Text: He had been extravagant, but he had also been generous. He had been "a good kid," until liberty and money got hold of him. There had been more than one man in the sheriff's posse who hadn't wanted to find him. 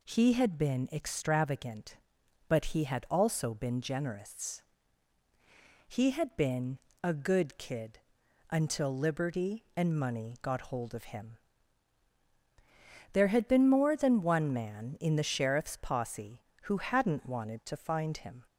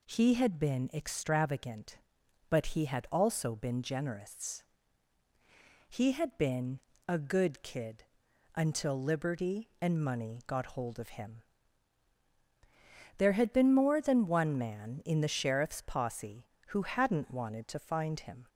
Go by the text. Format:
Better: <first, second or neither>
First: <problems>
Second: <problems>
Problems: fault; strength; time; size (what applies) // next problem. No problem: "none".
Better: neither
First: pauses between "been" and "a"; slight; at 6.7 s; 0.24 s long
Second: pauses between "been" and "a"; slight; at 6.8 s; 0.27 s long